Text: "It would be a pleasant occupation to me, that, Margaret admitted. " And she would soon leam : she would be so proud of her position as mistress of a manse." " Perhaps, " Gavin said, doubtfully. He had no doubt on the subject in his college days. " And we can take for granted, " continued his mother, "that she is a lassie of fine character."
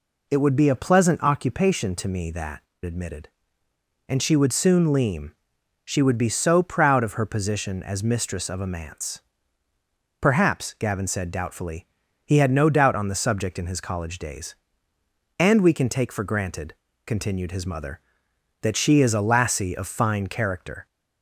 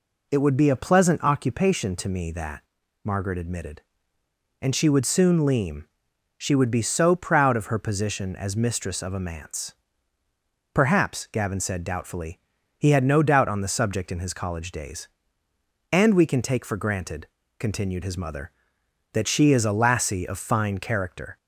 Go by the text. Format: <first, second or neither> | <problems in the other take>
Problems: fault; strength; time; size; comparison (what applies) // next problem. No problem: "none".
second | skips "Margaret"; at 2.7 s